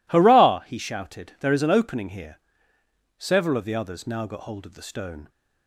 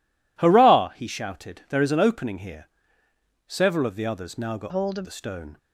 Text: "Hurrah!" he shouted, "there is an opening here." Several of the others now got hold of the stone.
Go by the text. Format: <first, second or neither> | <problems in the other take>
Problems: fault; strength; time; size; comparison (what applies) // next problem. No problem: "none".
first | changes voice from "hold" to "of"; from 4.6 to 5.0 s; 0.4 s long